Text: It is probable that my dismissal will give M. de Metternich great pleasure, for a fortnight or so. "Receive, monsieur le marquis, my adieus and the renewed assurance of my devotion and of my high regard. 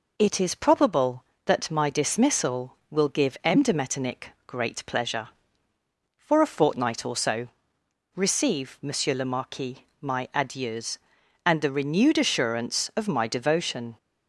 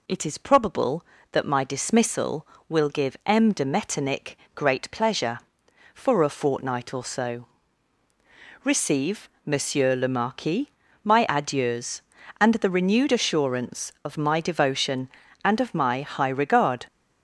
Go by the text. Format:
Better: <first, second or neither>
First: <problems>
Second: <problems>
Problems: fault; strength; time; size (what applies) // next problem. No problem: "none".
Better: second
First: pauses between "Metternich" and "great"; slight; at 4.2 s; 0.18 s long // stops before "and of my high regard"; at 13.9 s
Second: pauses between "Metternich" and "great"; slight; at 4.3 s; 0.18 s long